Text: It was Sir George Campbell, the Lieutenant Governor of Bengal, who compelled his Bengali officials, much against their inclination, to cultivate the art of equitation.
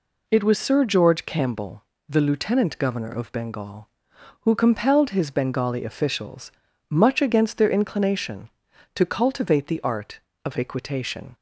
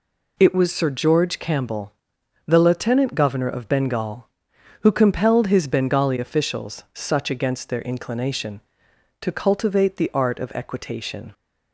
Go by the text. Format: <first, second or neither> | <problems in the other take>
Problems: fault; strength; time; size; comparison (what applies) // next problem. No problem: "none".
first | says "such" for "much"; at 6.9 s